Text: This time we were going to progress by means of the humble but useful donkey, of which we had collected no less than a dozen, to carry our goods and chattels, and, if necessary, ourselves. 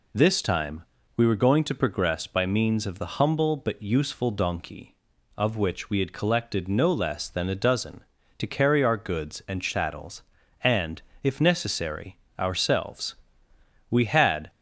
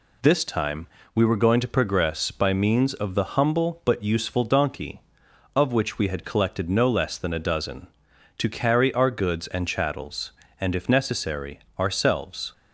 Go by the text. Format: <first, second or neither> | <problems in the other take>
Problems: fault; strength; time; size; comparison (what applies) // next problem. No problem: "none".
second | pauses between "time" and "we"; slight; at 0.8 s; 0.34 s long; slight in the second // goes on to say "We had"; from 13.9 s on; 0.58 s long